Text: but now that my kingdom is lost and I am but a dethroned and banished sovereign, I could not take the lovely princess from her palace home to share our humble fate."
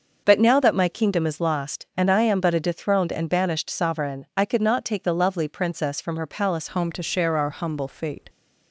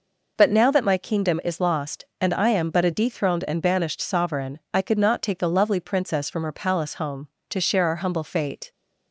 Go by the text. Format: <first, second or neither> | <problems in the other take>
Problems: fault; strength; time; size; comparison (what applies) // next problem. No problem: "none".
second | starts louder than the rest; until 1.2 s; 6 dB // changes voice at "home"; from 6.6 s on; 1.6 s long